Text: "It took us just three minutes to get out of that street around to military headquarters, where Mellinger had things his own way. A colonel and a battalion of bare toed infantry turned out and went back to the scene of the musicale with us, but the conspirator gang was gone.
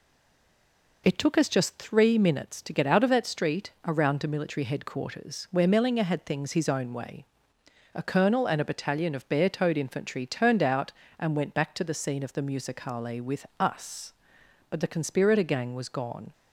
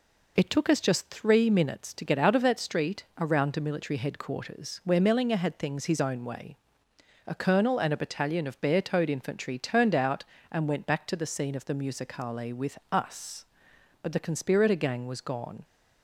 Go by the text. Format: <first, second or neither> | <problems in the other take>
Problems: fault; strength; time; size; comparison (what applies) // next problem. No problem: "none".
second | stays silent before the first word; until 1.0 s; 1.0 s long